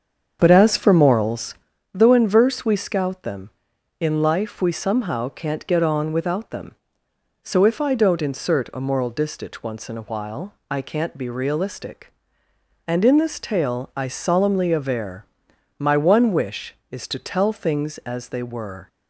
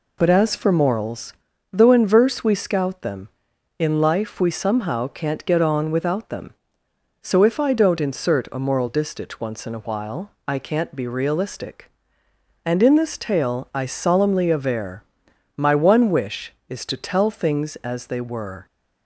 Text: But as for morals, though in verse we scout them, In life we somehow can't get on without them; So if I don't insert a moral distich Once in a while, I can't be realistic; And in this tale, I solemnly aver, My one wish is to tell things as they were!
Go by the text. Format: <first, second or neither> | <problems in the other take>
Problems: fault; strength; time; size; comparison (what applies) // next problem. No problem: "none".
second | starts louder than the rest; strong; until 1.8 s; 7.5 dB